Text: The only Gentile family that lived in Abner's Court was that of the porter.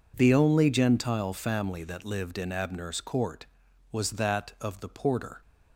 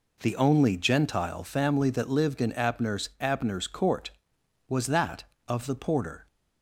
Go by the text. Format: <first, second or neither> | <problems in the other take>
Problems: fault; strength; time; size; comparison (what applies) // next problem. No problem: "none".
first | says "Abner's" twice; at 3.2 s